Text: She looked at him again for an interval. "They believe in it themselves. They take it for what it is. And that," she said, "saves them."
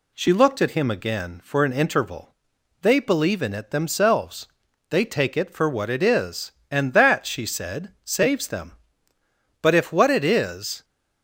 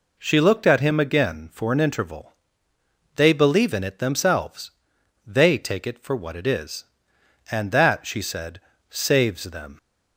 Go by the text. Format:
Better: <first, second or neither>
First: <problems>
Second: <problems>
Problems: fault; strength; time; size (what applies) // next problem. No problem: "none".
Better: second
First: goes on to say "But if what it is"; noticeable; from 9.5 s on; 1.2 s long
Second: none